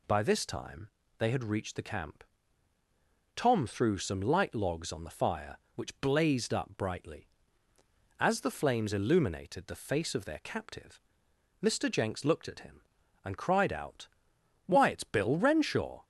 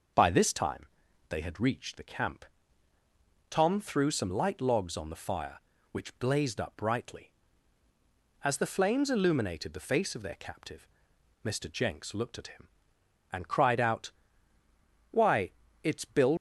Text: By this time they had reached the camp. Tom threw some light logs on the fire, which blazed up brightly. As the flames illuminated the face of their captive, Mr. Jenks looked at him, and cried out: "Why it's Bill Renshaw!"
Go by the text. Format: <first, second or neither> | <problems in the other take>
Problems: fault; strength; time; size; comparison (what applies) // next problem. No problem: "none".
first | pauses between "time" and "they"; at 0.8 s; 0.44 s long; slight in the first // pauses between "Why" and "it's"; slight; at 15.5 s; 0.30 s long // stops before "Renshaw"; at 16.3 s